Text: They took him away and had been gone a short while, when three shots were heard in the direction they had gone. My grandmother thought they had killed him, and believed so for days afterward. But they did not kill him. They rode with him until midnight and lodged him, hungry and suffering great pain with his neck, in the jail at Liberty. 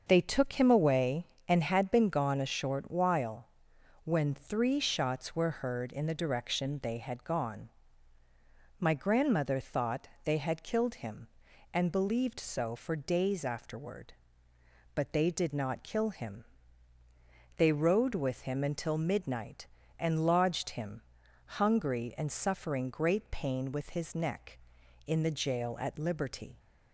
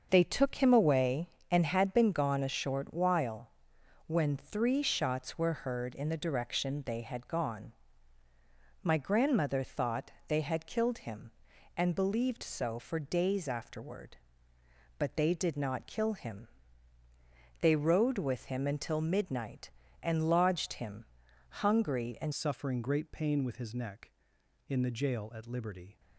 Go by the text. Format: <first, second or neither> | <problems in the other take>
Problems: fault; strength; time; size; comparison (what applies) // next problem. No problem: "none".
first | starts louder than the rest; until 1.1 s; 6.5 dB; also in the first // pauses between "thought" and "they"; slight; at 10.0 s; 0.16 s long; slight in the first // changes voice at "suffering"; from 22.3 s on; 3.6 s long